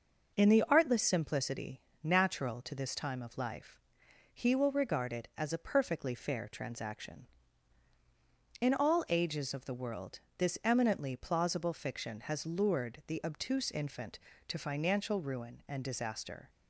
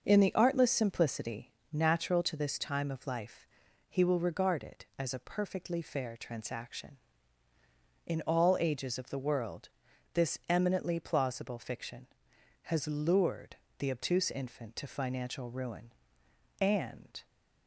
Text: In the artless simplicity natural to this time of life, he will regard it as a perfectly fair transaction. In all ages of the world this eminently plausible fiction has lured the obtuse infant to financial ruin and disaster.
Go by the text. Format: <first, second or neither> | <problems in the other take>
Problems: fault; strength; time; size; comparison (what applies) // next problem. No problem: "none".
first | starts louder than the rest; until 1.0 s; 6 dB // pauses between "simplicity" and "natural"; slight; at 1.5 s; 0.22 s long; slight in the first // pauses between "world" and "this"; at 9.6 s; 0.44 s long; slight in the first // pauses between "lured" and "the"; slight; at 13.5 s; 0.22 s long // stops before "disaster"; at 17.2 s